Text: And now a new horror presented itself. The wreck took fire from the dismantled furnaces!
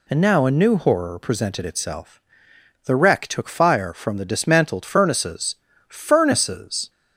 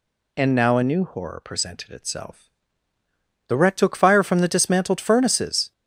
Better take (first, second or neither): second